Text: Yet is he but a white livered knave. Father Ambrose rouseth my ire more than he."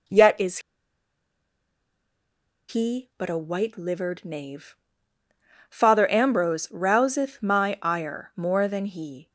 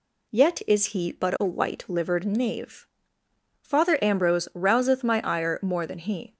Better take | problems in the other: second | pauses between "is" and "he"; strong; at 0.5 s; 2.1 s long

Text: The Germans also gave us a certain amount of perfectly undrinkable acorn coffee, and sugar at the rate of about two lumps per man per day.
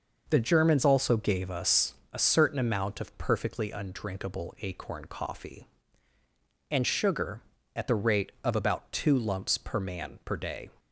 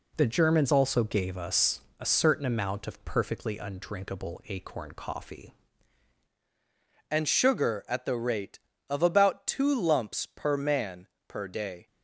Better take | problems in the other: first | pauses between "us" and "a"; slight; at 1.8 s; 0.18 s long; slight in the first // changes voice at "and"; from 7.1 s on; 4.7 s long // pauses between "man" and "per"; slight; at 11.0 s; 0.22 s long

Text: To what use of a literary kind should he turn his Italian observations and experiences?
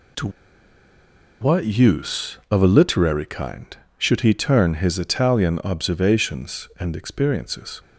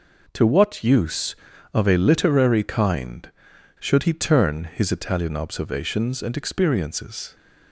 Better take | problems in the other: second | pauses between "To" and "what"; at 0.2 s; 1.1 s long

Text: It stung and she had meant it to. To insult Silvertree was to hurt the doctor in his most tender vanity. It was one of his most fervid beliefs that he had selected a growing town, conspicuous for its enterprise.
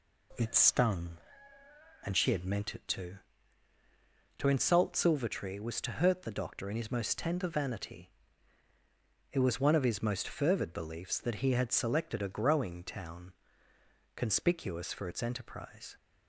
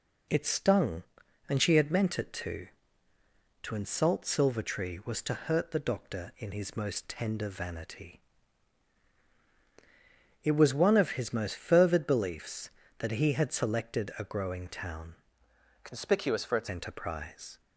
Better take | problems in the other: first | changes voice from "conspicuous" to "its"; from 15.8 to 16.6 s; 0.8 s long

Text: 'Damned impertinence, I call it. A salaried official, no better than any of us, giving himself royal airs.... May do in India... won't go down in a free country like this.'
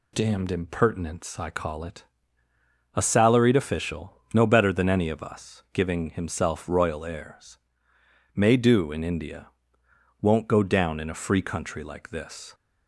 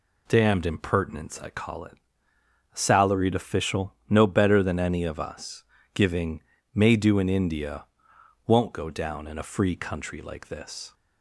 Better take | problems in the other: first | skips "himself royal airs"; at 6.5 s

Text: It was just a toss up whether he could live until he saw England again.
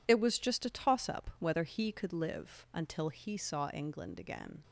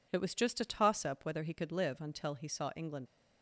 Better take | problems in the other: first | stops before "again"; at 3.0 s

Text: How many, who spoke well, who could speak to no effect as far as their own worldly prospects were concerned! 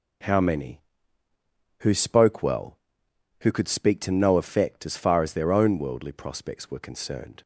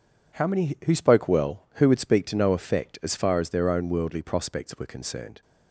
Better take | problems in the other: first | says "would" for "could"; at 1.8 s

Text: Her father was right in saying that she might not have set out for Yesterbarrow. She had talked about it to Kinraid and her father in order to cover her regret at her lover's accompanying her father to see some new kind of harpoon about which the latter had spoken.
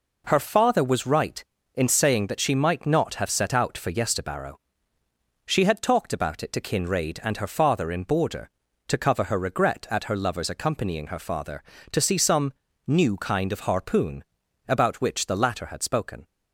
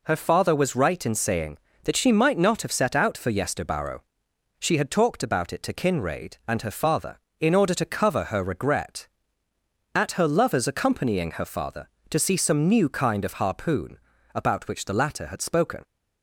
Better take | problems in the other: second | says "border" for "order"; at 8.0 s // pauses between "some" and "new"; slight; at 12.5 s; 0.34 s long // pauses between "harpoon" and "about"; at 14.2 s; 0.44 s long; also in the second

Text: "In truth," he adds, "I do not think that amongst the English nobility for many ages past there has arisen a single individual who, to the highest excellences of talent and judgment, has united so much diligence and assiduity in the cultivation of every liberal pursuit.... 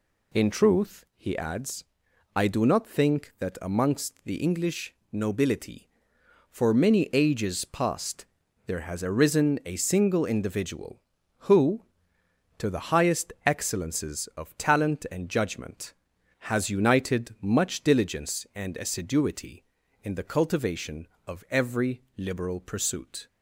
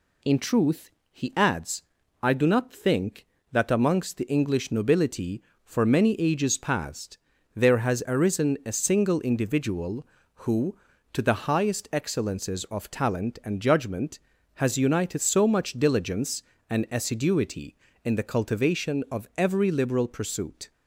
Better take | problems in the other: second | pauses between "English" and "nobility"; slight; at 4.9 s; 0.18 s long // pauses between "past" and "there"; at 8.2 s; 0.42 s long; also in the second // skips "so"; at 17.3 s

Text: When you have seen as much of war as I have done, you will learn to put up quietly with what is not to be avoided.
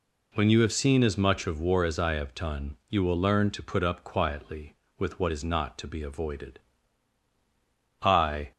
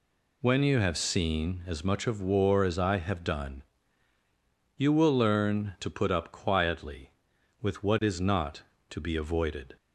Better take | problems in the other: second | goes on to say "I"; from 8.0 s on; 0.50 s long

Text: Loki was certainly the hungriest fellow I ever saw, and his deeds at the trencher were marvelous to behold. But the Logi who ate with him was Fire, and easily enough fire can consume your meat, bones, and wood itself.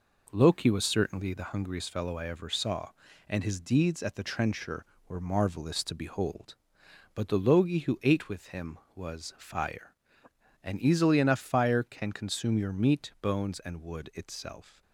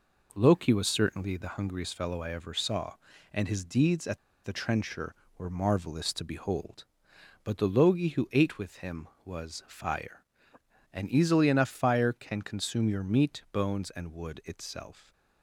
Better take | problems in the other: first | pauses between "at" and "the"; slight; at 4.1 s; 0.27 s long

